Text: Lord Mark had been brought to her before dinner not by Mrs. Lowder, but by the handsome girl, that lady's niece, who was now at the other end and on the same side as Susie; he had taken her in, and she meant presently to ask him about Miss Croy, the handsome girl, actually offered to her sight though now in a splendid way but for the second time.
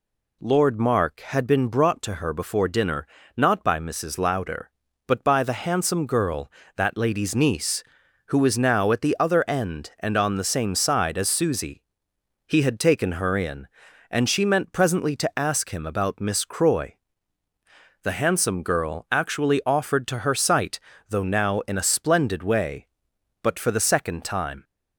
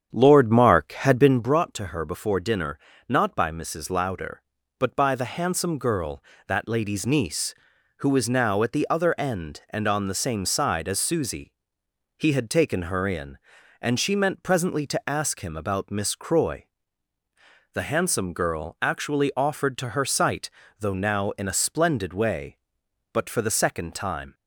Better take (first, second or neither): first